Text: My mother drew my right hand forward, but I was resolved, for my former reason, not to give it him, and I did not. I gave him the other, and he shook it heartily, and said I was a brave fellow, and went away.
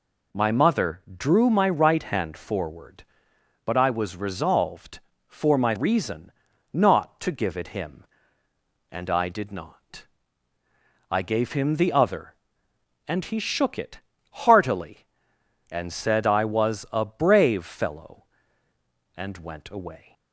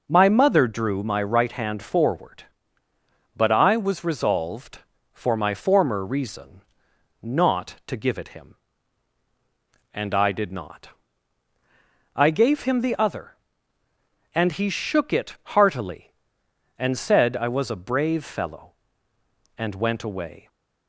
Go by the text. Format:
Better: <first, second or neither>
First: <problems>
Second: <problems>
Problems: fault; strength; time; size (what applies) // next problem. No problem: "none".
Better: second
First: pauses between "mother" and "drew"; slight; at 1.0 s; 0.18 s long // skips "former"; at 5.7 s // pauses between "it" and "heartily"; slight; at 13.9 s; 0.32 s long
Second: none